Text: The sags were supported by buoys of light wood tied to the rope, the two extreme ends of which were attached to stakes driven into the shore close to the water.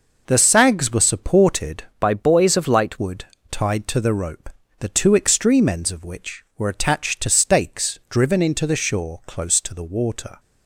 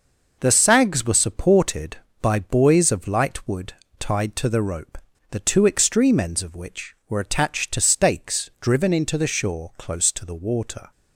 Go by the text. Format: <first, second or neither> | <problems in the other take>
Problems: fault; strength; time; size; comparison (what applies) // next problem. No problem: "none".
second | changes voice from "by" to "light"; from 1.9 to 2.9 s; 1.0 s long // pauses between "wood" and "tied"; slight; at 3.2 s; 0.26 s long; slight in the second